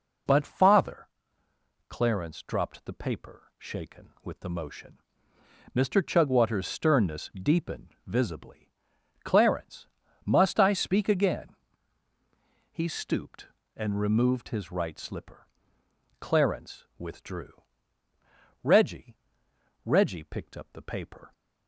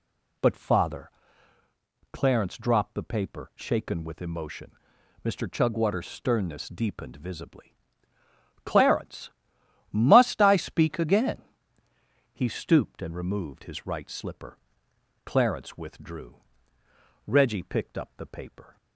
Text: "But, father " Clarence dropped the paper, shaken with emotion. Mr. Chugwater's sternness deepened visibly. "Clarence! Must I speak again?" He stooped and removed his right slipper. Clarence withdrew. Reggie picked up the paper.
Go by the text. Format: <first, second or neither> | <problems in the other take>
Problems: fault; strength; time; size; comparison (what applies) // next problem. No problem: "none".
second | says "Reggie" twice; at 19.8 s